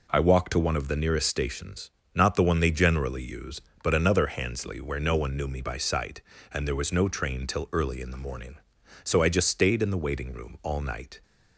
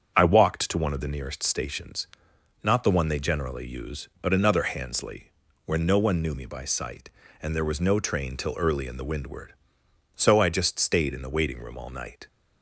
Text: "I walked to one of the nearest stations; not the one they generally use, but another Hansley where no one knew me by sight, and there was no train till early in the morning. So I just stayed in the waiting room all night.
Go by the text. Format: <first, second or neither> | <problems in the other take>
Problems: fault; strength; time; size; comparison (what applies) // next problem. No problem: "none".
first | starts louder than the rest; strong; until 1.1 s; 7.5 dB // pauses between "Hansley" and "where"; slight; at 5.3 s; 0.32 s long // says "windward" for "morning"; at 9.0 s